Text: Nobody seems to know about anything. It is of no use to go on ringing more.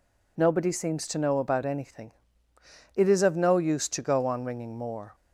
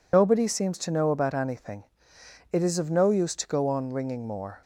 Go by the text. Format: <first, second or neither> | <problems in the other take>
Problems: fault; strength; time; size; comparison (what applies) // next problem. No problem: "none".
first | loses the start of "Nobody"; at 0.1 s; 85 ms